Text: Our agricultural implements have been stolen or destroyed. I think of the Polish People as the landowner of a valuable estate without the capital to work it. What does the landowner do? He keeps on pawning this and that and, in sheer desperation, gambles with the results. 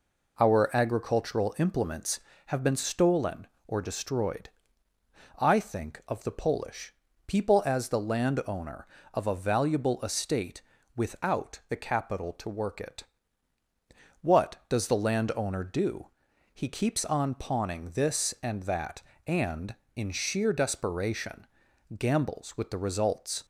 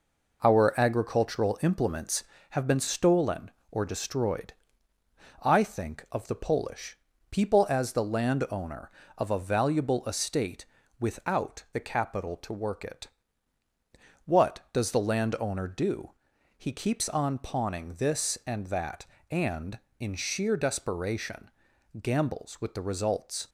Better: first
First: pauses between "Polish" and "People"; slight; at 6.9 s; 0.34 s long // pauses between "estate" and "without"; slight; at 10.6 s; 0.34 s long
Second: gets quieter; noticeable; throughout; 5 dB // pauses between "Polish" and "People"; slight; at 6.9 s; 0.34 s long // pauses between "estate" and "without"; slight; at 10.6 s; 0.34 s long

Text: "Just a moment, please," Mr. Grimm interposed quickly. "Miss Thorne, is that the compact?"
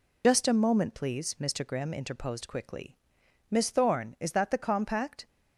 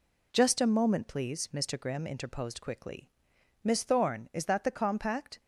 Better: second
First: loses the start of "Just"; at 0.2 s; 60 ms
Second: none

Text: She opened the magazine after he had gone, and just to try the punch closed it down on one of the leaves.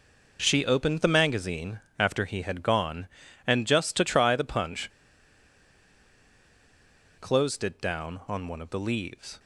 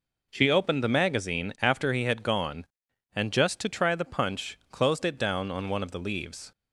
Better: second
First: pauses between "magazine" and "after"; slight; at 1.8 s; 0.18 s long // pauses between "punch" and "closed"; strong; at 4.8 s; 2.3 s long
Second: none

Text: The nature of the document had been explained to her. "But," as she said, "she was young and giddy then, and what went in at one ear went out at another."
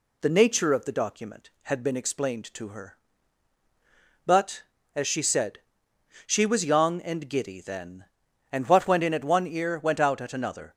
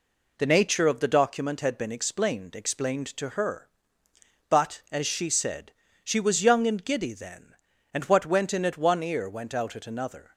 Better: first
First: none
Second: says "explained" twice; at 2.5 s

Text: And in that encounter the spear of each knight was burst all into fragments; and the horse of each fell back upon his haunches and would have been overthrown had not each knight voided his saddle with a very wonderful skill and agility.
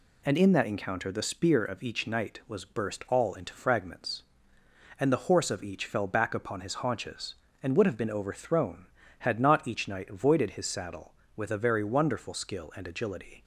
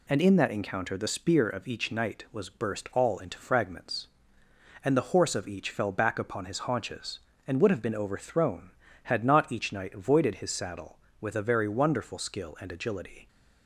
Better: neither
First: none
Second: none

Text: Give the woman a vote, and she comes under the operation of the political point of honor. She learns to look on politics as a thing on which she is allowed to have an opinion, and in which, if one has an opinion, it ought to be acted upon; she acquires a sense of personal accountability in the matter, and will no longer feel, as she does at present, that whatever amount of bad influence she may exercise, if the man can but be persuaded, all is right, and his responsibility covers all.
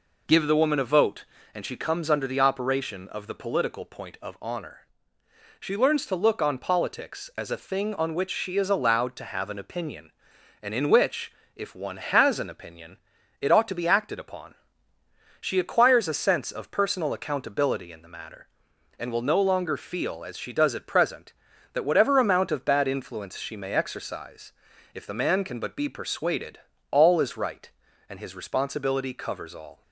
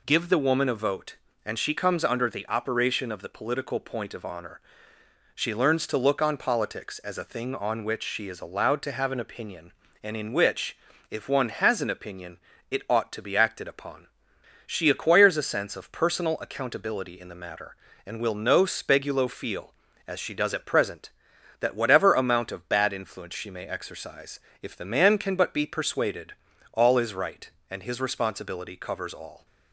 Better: first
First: none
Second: says "spegulo" for "longer"; at 18.6 s

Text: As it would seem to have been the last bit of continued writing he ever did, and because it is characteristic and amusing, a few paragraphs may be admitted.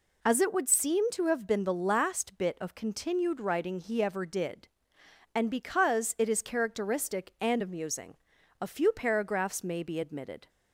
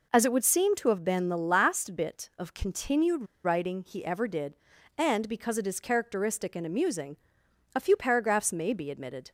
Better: first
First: none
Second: pauses between "continued" and "writing"; slight; at 3.2 s; 0.21 s long

